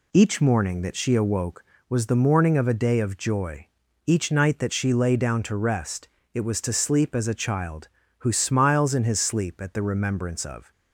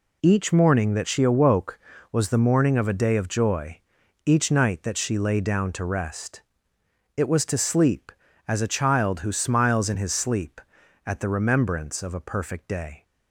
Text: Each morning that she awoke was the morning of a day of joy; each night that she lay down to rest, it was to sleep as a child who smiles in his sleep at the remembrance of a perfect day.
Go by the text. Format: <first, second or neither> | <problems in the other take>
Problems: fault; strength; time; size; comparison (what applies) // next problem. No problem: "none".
second | stops before "a perfect day"; at 10.7 s